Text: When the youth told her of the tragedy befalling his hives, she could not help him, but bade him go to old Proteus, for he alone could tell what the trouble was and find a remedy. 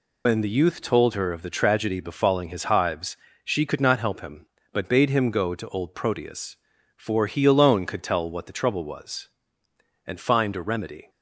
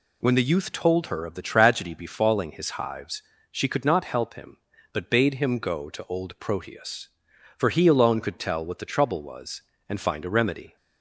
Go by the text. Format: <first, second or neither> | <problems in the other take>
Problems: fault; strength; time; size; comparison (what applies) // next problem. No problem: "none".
second | loses the start of "When"; at 0.2 s; 85 ms